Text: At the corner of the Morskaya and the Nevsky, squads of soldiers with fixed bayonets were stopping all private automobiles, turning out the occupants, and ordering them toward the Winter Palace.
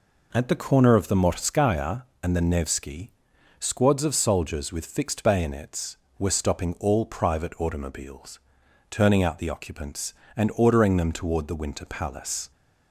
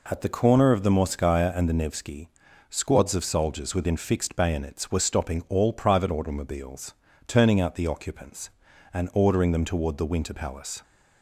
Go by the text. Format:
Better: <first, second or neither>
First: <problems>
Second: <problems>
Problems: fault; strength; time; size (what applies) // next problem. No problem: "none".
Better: first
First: none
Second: says "within" for "with"; at 3.7 s